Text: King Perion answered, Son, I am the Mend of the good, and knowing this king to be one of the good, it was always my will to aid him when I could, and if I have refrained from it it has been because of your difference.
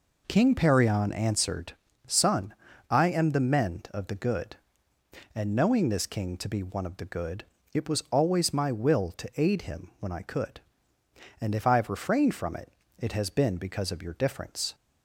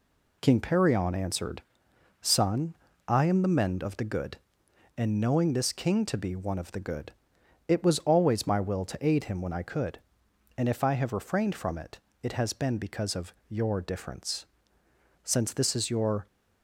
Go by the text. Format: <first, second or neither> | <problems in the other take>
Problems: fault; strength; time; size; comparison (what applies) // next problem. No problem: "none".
first | pauses between "it" and "it"; slight; at 11.9 s; 0.24 s long; slight in the first // pauses between "of" and "your"; slight; at 13.3 s; 0.16 s long // goes on to say "Since this is your"; noticeable; from 15.2 s on; 1.0 s long